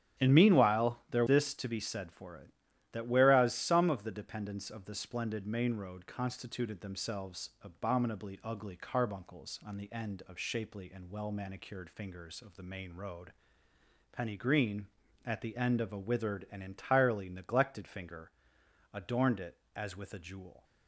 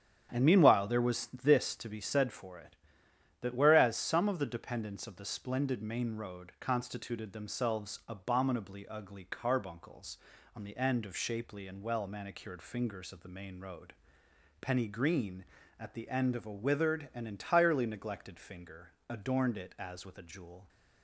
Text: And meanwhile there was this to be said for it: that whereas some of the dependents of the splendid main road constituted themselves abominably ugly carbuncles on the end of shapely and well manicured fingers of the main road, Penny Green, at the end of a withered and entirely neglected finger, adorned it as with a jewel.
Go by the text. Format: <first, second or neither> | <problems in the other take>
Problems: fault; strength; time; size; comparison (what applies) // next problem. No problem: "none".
second | starts louder than the rest; strong; until 1.2 s; 9.5 dB; strong in the second // skips "was"; at 1.2 s